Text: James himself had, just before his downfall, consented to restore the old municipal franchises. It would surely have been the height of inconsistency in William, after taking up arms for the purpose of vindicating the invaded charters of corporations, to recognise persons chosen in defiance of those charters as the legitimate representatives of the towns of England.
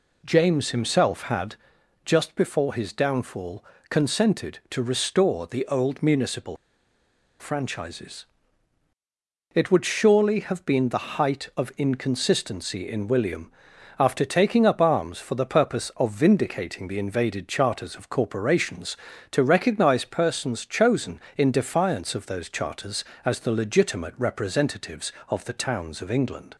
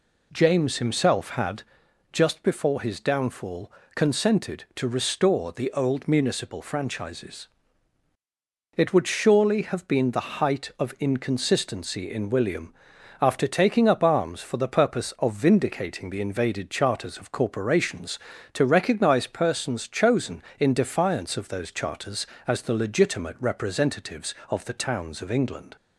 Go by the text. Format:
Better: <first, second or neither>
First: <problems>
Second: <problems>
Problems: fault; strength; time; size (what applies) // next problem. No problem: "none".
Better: second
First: pauses between "municipal" and "franchises"; noticeable; at 6.5 s; 0.83 s long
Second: none